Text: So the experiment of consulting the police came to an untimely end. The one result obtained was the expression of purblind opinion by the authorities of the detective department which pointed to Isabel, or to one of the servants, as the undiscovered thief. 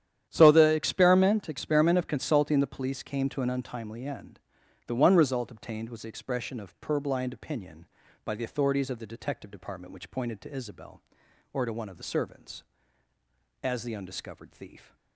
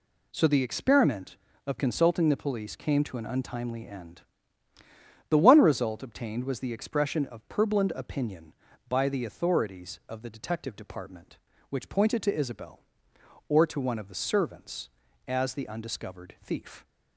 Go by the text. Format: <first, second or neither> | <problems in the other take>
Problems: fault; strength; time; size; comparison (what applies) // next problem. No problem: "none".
second | starts louder than the rest; strong; until 1.3 s; 10.5 dB // says "experiment" twice; at 1.4 s